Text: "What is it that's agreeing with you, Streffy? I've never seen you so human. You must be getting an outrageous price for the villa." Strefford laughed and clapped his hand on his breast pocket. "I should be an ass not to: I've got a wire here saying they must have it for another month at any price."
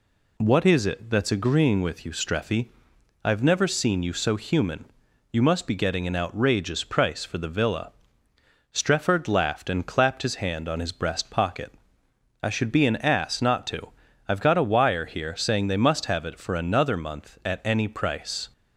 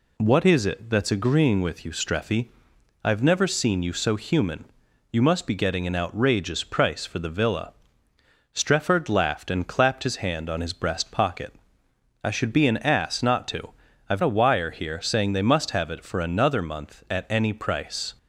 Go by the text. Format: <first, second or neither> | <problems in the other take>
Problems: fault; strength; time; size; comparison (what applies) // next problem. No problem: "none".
first | skips "got"; at 14.2 s